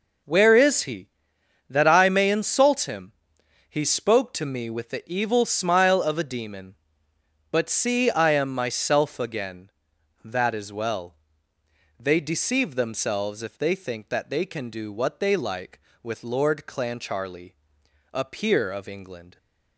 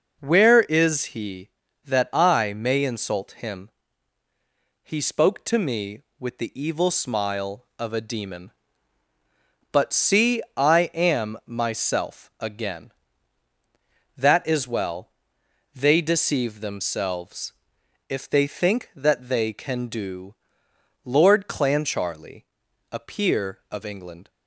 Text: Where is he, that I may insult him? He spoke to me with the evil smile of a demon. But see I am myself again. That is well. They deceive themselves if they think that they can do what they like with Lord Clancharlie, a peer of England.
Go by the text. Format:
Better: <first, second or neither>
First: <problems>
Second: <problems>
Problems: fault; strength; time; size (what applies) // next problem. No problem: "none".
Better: first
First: none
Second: pauses between "themselves" and "if"; noticeable; at 17.5 s; 0.56 s long // skips "what they like with"; at 20.6 s